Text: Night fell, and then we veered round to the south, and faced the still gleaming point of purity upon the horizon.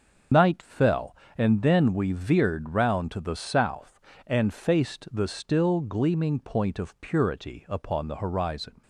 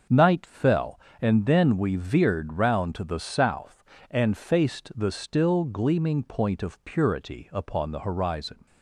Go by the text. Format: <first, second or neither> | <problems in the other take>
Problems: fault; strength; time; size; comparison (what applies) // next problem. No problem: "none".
second | loses the start of "Night"; at 0.3 s; 55 ms // starts louder than the rest; until 1.5 s; 6.5 dB; also in the second